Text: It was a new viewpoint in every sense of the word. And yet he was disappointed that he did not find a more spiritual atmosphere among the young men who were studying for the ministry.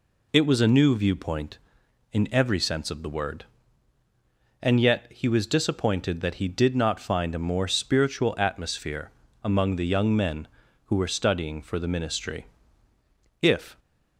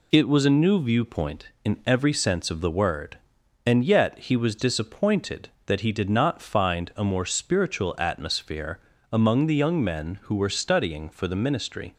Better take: second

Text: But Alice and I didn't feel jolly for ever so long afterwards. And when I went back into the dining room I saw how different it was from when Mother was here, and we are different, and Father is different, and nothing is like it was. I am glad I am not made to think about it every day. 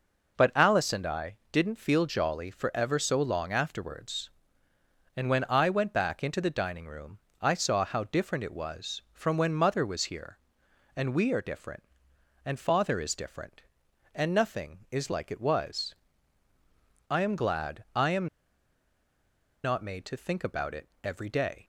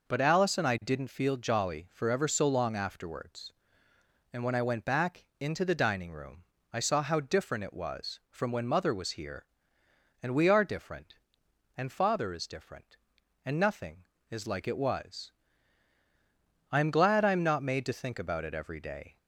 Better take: second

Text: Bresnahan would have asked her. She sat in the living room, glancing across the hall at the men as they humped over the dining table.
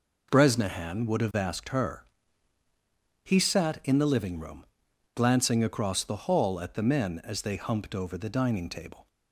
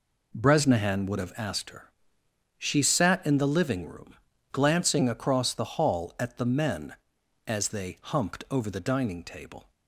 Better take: second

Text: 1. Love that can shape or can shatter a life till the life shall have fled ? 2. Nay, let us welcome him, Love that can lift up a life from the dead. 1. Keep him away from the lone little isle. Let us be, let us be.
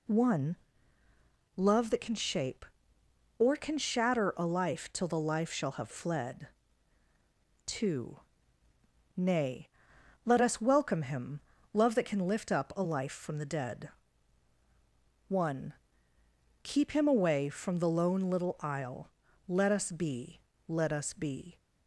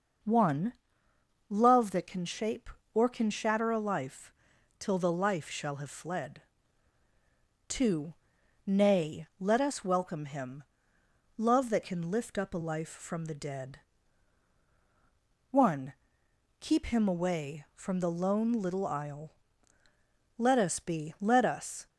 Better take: first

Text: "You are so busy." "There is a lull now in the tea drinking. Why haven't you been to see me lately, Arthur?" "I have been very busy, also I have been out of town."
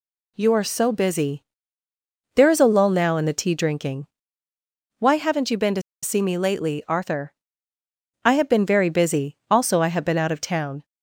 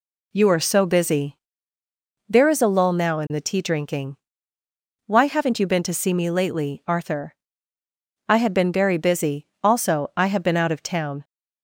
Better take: second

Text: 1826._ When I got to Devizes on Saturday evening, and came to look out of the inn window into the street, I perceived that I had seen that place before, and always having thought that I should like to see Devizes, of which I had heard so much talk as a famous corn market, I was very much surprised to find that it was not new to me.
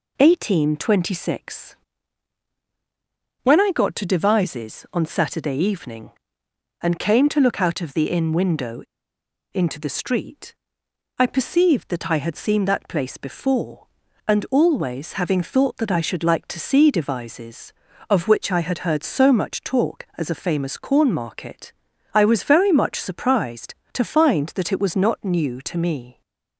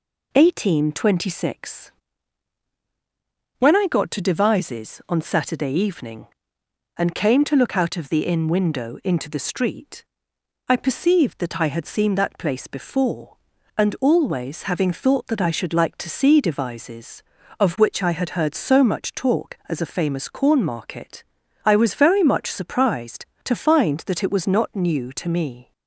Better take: second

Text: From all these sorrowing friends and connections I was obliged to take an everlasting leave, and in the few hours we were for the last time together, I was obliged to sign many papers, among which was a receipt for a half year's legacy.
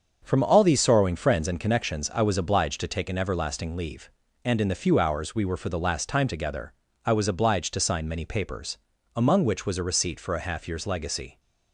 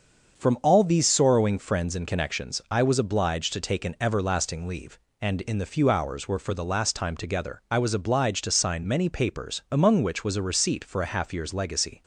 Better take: first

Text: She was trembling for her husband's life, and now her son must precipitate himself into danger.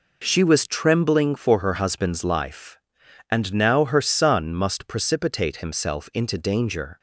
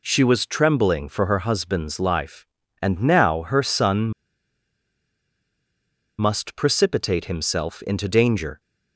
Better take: first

